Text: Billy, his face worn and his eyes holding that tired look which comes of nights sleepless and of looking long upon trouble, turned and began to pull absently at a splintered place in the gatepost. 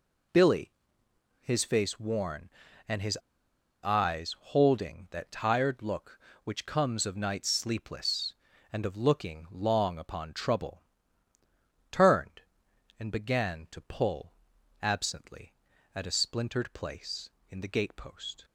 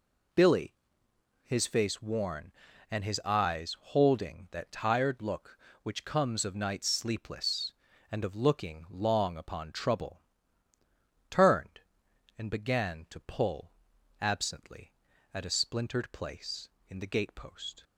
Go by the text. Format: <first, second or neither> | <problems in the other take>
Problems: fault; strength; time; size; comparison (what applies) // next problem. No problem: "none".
second | pauses between "his" and "eyes"; noticeable; at 3.1 s; 0.65 s long // pauses between "pull" and "absently"; noticeable; at 14.3 s; 0.50 s long; noticeable in the second